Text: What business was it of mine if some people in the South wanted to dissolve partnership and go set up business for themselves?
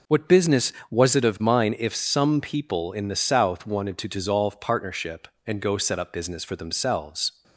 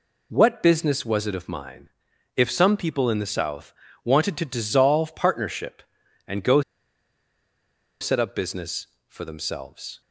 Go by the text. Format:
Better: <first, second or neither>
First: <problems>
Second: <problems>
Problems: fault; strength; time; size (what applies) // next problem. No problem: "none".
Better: first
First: none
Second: pauses between "mine" and "if"; noticeable; at 1.8 s; 0.48 s long // pauses between "South" and "wanted"; slight; at 3.7 s; 0.32 s long // pauses between "go" and "set"; strong; at 6.6 s; 1.3 s long